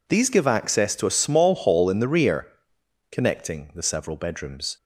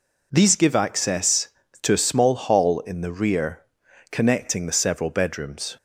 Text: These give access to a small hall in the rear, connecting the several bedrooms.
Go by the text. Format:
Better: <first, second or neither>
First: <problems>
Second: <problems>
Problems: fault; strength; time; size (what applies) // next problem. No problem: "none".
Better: neither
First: none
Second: none